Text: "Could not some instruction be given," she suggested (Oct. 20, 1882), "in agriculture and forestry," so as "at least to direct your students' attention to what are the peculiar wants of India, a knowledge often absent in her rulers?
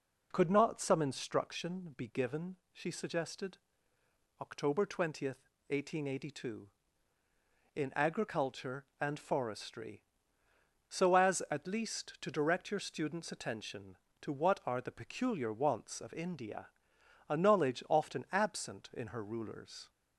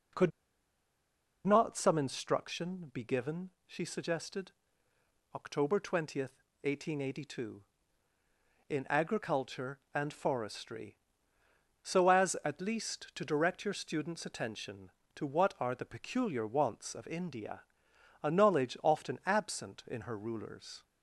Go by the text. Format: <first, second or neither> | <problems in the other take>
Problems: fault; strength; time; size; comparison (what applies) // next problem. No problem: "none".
first | pauses between "Could" and "not"; at 0.3 s; 1.1 s long